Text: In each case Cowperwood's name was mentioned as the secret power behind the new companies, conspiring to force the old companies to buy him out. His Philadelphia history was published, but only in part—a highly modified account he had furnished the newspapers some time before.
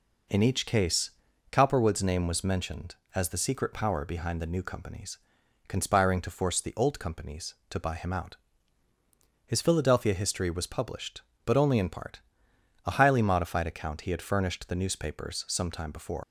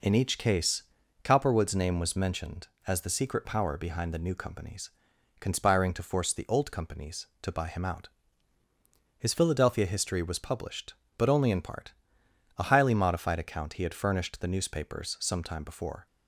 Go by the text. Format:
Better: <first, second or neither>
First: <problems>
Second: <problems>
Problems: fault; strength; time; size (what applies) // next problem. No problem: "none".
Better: second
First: pauses between "case" and "Cowperwood's"; at 1.0 s; 0.42 s long // leaves "before" unfinished; at 16.2 s; 105 ms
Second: pauses between "case" and "Cowperwood's"; at 0.8 s; 0.42 s long